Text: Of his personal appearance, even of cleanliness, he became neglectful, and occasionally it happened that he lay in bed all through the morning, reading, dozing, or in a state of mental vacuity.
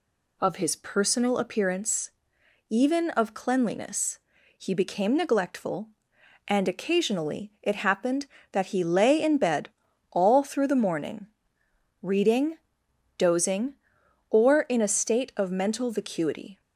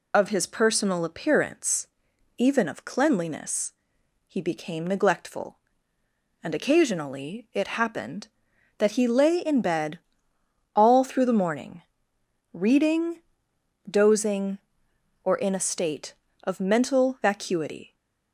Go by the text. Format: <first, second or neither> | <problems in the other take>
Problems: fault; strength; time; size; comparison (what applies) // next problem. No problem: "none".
first | loses the start of "Of"; at 0.1 s; 45 ms // pauses between "bed" and "all"; noticeable; at 9.9 s; 0.76 s long; also in the first